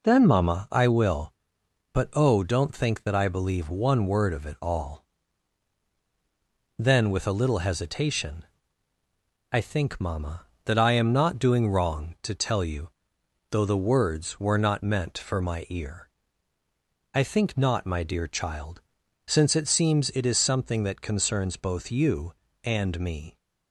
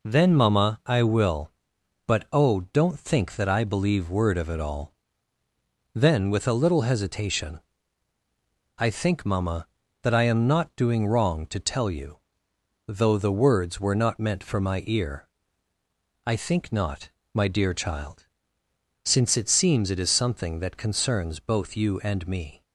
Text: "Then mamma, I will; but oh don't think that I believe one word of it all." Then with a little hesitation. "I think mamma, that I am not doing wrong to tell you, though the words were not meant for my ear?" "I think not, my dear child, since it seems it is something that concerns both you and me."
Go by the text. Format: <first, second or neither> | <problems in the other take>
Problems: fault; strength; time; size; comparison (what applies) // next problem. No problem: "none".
first | skips "one"; at 4.0 s